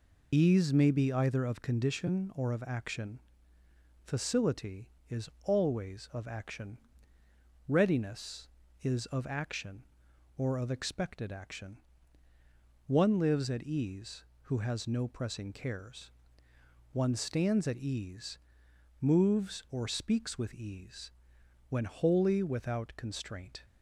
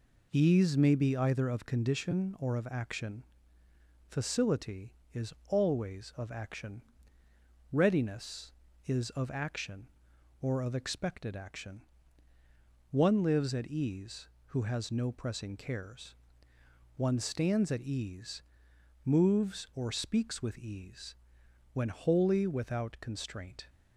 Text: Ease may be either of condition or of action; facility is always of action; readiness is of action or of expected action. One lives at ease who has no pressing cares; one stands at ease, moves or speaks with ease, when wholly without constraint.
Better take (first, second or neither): second